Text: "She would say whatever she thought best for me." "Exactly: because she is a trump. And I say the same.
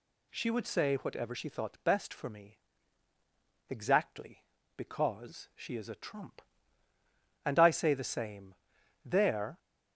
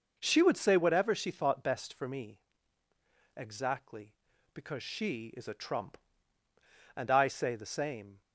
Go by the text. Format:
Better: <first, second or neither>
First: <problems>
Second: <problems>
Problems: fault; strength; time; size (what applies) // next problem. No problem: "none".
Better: second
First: goes on to say "There"; from 9.0 s on; 0.54 s long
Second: none